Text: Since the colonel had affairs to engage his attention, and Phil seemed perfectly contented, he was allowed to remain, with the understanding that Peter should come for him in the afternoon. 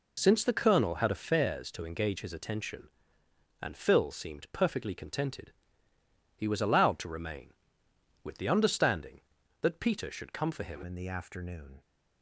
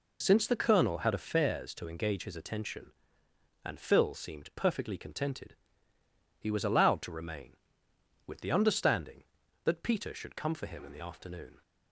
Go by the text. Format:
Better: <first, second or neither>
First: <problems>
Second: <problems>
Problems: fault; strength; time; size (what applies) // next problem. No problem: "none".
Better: second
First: changes voice at "in"; from 10.8 s on; 1.0 s long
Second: none